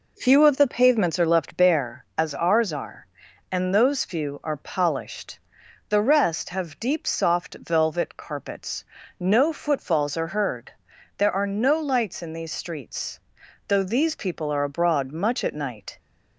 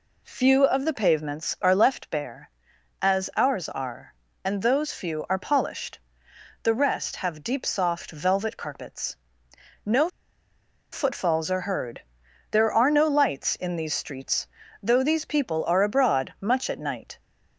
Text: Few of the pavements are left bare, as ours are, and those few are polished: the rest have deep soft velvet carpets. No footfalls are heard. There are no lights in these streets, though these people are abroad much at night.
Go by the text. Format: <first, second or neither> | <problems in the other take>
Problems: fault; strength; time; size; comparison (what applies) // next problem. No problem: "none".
first | pauses between "No" and "footfalls"; noticeable; at 10.0 s; 0.85 s long